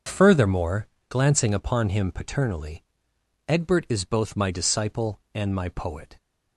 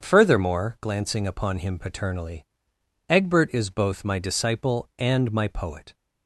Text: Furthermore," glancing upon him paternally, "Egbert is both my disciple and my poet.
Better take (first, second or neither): neither